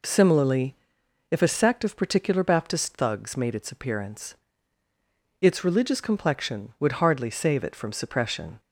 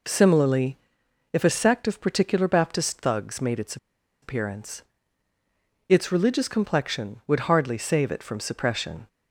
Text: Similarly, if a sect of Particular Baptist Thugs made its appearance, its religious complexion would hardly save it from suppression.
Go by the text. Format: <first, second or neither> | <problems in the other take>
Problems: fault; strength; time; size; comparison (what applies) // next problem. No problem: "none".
first | pauses between "its" and "appearance"; noticeable; at 3.7 s; 0.46 s long